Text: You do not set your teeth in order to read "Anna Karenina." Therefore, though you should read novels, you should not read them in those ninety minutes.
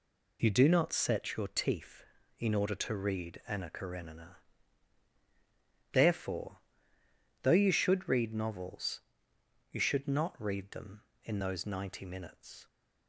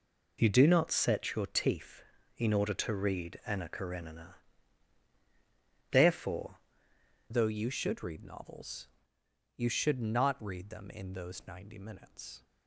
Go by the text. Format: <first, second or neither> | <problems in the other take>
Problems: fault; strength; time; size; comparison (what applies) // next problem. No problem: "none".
first | changes voice at "though"; from 7.3 s on; 5.1 s long